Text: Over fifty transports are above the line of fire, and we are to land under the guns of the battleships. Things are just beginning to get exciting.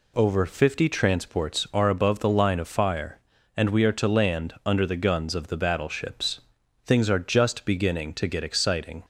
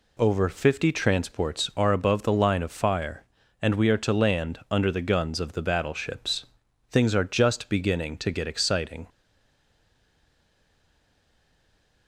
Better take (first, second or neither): first